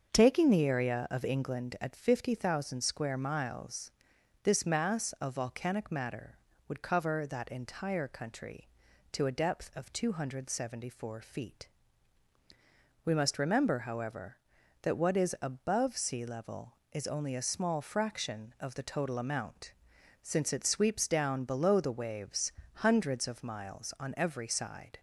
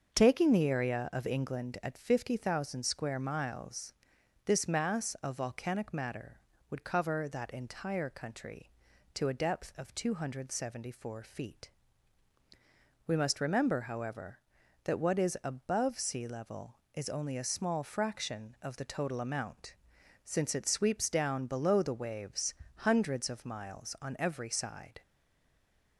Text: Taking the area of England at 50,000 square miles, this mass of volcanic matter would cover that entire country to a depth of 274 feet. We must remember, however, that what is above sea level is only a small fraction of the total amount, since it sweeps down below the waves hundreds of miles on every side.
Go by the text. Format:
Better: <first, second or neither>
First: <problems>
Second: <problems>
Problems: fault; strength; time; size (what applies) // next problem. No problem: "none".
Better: first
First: starts louder than the rest; until 1.1 s; 6.5 dB // pauses between "waves" and "hundreds"; slight; at 22.5 s; 0.24 s long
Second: starts louder than the rest; until 1.2 s; 6.5 dB // pauses between "waves" and "hundreds"; slight; at 22.5 s; 0.24 s long // stays silent after the last word; from 25.0 s on; 0.9 s long